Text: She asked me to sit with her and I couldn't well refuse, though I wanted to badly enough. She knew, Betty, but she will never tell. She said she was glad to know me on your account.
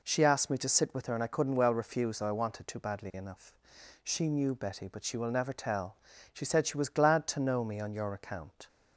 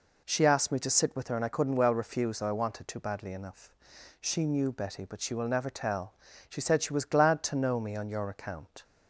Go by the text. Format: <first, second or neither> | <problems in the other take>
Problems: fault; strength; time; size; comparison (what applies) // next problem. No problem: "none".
neither | none